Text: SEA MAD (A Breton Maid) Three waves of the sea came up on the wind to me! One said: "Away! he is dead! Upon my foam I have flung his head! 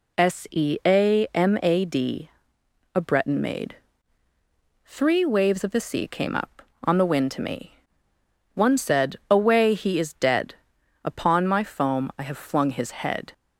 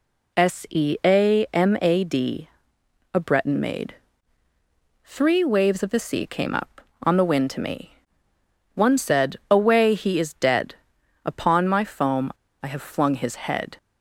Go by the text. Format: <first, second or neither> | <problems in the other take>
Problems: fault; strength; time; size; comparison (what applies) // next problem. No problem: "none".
first | pauses between "foam" and "I"; slight; at 12.3 s; 0.29 s long